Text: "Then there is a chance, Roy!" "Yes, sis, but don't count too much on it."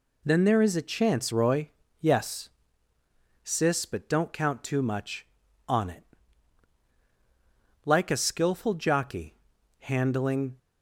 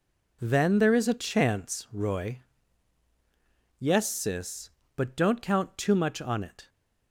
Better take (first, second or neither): second